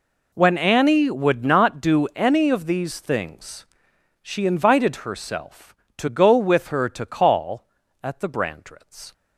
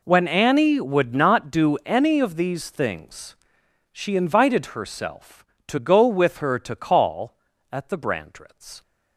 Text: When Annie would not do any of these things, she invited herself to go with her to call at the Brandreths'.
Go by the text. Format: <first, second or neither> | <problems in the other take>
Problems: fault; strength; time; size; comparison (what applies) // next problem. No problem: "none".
neither | none